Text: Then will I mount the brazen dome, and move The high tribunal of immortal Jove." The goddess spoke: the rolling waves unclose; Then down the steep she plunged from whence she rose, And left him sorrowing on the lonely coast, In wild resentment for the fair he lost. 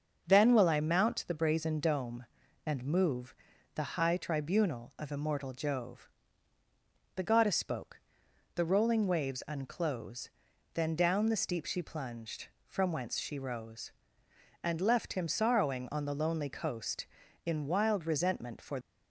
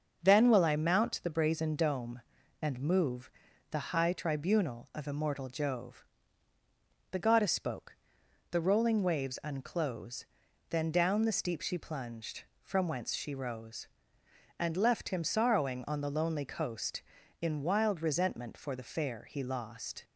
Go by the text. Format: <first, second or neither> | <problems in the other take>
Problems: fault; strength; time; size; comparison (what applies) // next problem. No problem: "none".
second | starts louder than the rest; until 1.2 s; 6.5 dB; also in the second // pauses between "move" and "The"; at 3.3 s; 0.40 s long; also in the second // stops before "the fair he lost"; at 18.8 s